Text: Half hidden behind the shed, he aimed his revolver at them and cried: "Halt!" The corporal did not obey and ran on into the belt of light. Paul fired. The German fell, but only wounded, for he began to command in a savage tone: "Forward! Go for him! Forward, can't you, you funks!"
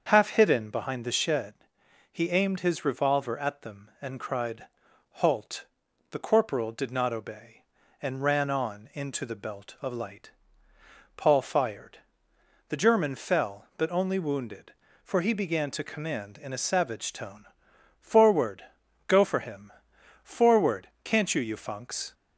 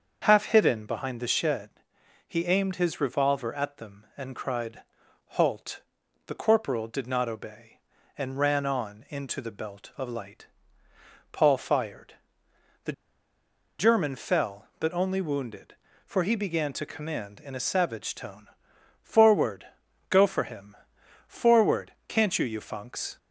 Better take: first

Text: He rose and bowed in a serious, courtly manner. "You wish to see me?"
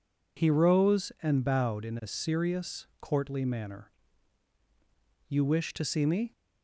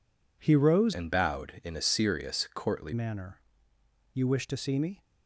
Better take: first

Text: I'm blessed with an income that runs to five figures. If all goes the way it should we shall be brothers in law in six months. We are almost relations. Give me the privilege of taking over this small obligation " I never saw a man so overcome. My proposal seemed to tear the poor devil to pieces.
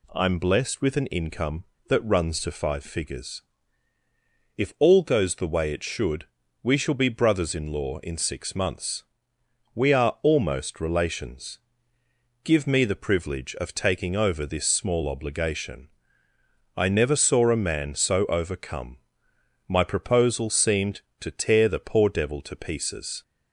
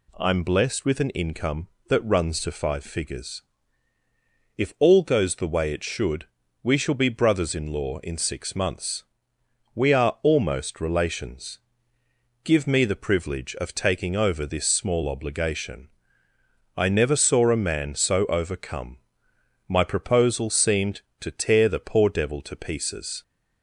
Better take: neither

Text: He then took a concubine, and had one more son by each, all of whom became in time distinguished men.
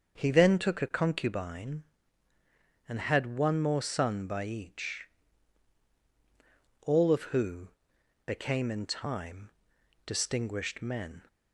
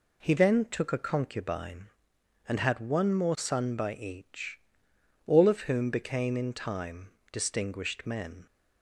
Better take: second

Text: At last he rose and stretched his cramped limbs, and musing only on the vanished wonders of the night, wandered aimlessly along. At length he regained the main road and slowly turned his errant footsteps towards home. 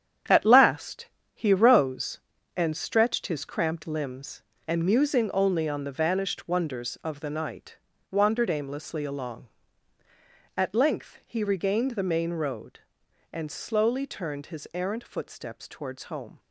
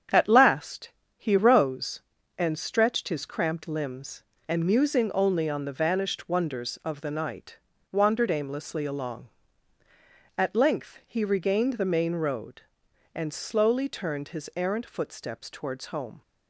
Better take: second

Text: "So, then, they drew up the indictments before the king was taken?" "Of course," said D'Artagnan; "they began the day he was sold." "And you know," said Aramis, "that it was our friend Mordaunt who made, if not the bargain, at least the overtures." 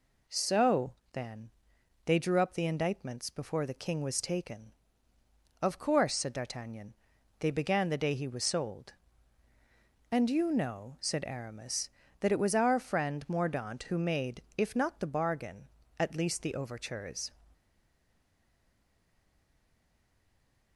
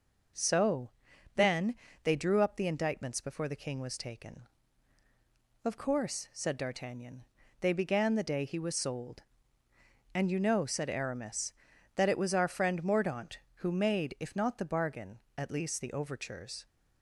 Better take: second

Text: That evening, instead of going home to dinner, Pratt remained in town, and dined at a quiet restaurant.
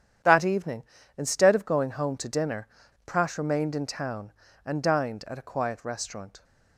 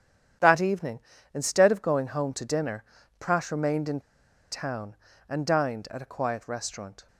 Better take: first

